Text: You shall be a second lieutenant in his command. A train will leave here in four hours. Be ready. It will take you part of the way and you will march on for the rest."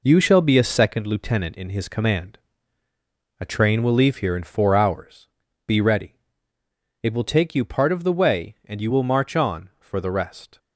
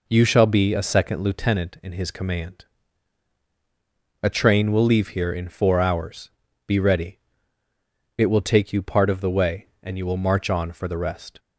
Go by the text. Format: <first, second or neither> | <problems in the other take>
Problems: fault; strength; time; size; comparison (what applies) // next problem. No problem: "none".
second | gets quieter; throughout; 7 dB